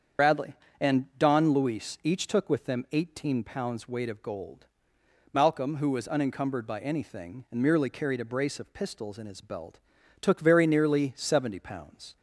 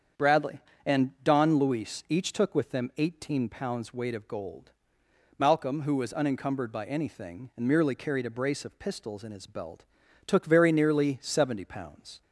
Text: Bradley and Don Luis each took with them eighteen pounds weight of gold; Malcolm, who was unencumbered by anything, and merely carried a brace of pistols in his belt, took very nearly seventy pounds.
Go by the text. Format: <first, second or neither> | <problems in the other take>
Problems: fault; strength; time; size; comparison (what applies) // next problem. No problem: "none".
second | loses the start of "Bradley"; at 0.1 s; 70 ms // starts louder than the rest; strong; until 1.5 s; 7.5 dB; strong in the second